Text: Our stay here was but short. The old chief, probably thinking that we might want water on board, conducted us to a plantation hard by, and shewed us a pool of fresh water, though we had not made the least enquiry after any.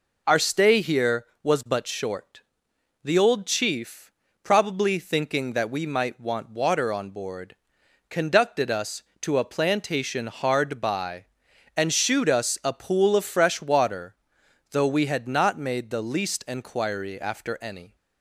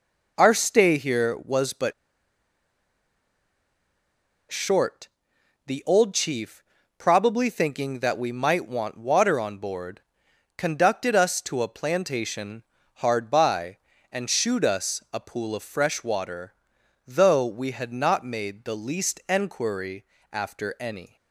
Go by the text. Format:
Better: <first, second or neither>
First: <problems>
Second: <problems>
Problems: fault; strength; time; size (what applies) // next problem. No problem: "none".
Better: first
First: none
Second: pauses between "but" and "short"; strong; at 1.9 s; 2.5 s long // pauses between "plantation" and "hard"; slight; at 12.6 s; 0.32 s long // pauses between "enquiry" and "after"; slight; at 20.0 s; 0.26 s long